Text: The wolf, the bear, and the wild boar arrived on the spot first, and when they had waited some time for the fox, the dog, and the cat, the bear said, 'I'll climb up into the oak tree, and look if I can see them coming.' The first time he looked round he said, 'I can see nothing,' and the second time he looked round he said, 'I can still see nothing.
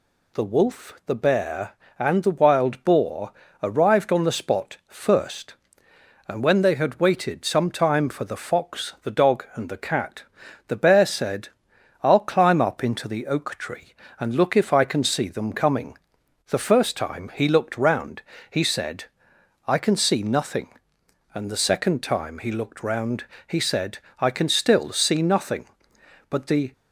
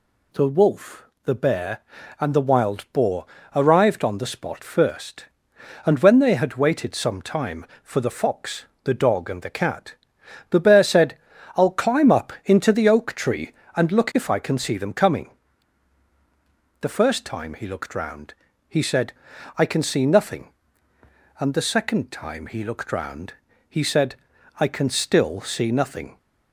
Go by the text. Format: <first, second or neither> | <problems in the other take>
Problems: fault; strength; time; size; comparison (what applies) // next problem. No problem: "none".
second | pauses between "boar" and "arrived"; slight; at 3.3 s; 0.30 s long; slight in the second // pauses between "round" and "he"; slight; at 18.2 s; 0.28 s long; slight in the second // pauses between "round" and "he"; slight; at 23.2 s; 0.24 s long; slight in the second // goes on to say "But the"; slight; from 26.2 s on; 0.44 s long